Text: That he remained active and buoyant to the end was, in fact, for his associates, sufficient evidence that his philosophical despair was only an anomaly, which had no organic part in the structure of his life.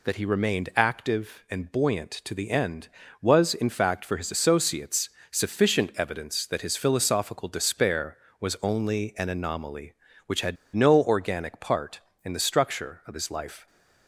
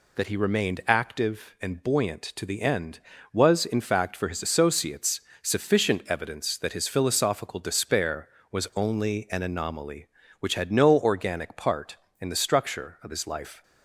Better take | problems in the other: second | pauses between "had" and "no"; slight; at 10.5 s; 0.20 s long

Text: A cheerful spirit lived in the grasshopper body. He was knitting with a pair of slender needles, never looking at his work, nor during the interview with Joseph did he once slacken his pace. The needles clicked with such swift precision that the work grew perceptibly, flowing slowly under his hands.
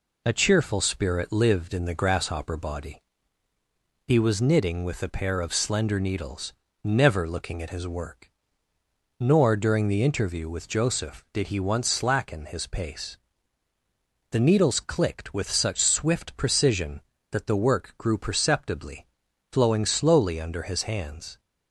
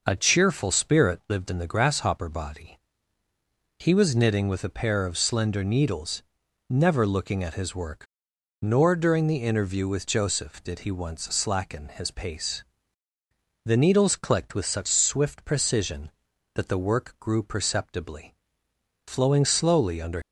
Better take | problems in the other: first | stops before "his hands"; at 20.2 s

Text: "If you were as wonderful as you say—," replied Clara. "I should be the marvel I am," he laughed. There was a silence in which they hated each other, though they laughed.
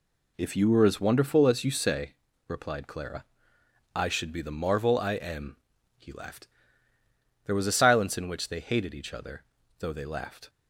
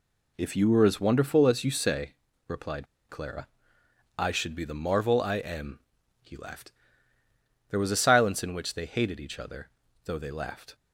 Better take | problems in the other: first | pauses between "replied" and "Clara"; slight; at 2.8 s; 0.24 s long

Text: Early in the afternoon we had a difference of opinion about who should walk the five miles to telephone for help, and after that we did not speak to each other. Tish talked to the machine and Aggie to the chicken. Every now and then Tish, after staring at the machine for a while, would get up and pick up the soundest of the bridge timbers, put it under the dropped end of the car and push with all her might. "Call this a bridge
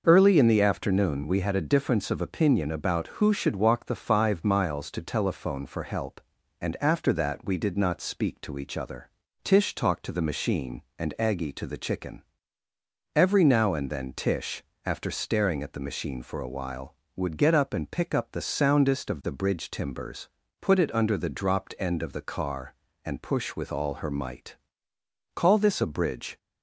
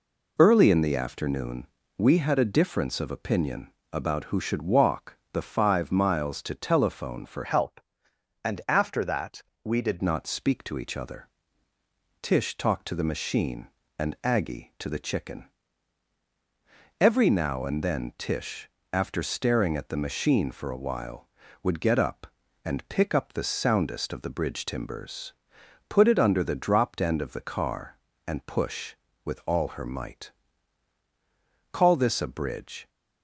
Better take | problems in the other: first | pauses between "afternoon" and "we"; slight; at 1.6 s; 0.32 s long // pauses between "opinion" and "about"; slight; at 3.7 s; 0.20 s long // pauses between "walk" and "the"; slight; at 5.1 s; 0.16 s long // changes voice from "help" to "did"; from 7.4 to 10.0 s; 2.6 s long // pauses between "that" and "we"; slight; at 9.4 s; 0.22 s long

